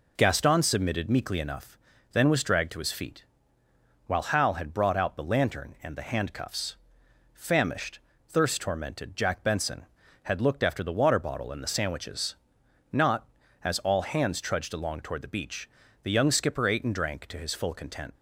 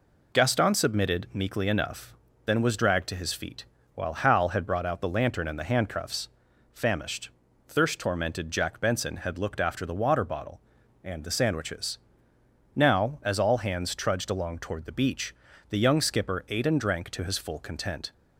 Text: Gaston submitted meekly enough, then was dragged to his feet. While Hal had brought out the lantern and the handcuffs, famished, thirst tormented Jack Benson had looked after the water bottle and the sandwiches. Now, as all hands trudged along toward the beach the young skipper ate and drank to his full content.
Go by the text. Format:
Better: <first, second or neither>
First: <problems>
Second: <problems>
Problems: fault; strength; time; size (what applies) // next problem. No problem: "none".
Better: second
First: says "Not" for "Now"; at 12.9 s // pauses between "beach" and "the"; at 15.6 s; 0.36 s long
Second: pauses between "beach" and "the"; slight; at 15.3 s; 0.36 s long